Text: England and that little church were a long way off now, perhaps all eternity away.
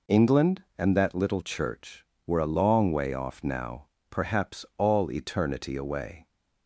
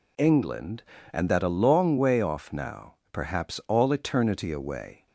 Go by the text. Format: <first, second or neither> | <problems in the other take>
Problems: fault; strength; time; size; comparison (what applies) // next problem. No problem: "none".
first | skips "little church were"; at 1.4 s